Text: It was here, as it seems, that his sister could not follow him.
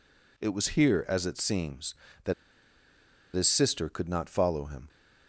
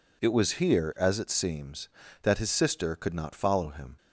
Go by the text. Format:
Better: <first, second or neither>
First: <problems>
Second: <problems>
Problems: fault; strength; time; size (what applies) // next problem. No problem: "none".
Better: second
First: pauses between "that" and "his"; at 2.3 s; 1.0 s long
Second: none